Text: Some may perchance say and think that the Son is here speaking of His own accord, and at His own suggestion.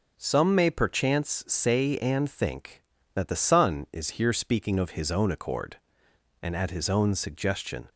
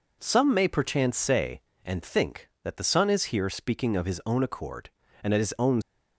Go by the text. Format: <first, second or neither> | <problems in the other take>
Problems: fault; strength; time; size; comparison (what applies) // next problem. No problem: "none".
first | stops before "suggestion"; at 5.8 s